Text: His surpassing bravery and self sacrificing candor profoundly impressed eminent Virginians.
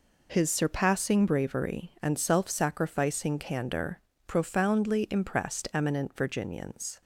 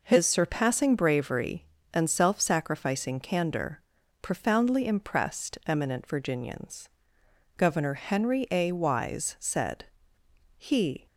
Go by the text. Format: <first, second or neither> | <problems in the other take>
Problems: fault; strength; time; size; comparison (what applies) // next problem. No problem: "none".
first | pauses between "candor" and "profoundly"; at 3.8 s; 0.40 s long; slight in the first // goes on to say "Governor Henry A Wise said He"; strong; from 7.5 s on; 3.5 s long